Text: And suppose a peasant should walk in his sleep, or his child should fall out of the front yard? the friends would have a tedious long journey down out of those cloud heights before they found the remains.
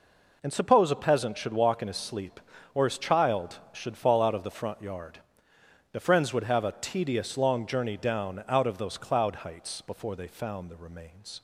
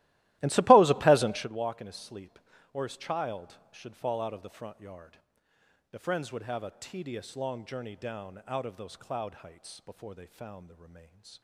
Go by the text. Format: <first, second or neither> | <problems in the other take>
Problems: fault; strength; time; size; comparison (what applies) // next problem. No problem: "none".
first | starts louder than the rest; strong; until 1.5 s; 16.5 dB